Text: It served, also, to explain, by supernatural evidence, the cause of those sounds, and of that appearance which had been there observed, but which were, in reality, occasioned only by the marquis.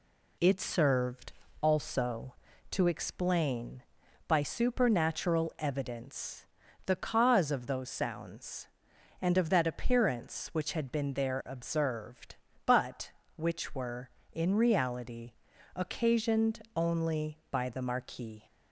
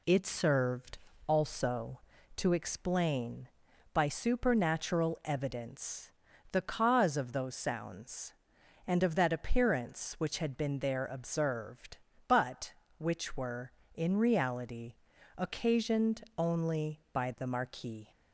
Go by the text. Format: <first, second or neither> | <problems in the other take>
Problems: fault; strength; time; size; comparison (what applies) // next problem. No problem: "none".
neither | pauses between "occasioned" and "only"; slight; the same in both